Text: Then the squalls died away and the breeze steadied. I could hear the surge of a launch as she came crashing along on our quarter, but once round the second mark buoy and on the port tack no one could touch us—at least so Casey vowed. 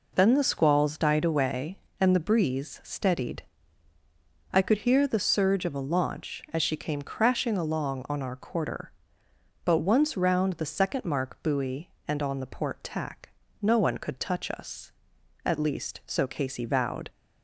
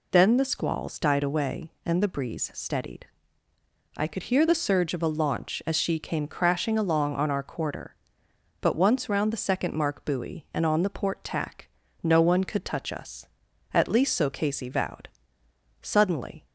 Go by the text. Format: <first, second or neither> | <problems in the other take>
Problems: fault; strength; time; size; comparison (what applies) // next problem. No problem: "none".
first | pauses between "tack" and "no"; slight; at 11.6 s; 0.34 s long; slight in the first // goes on to say "Suddenly"; noticeable; from 15.8 s on; 0.66 s long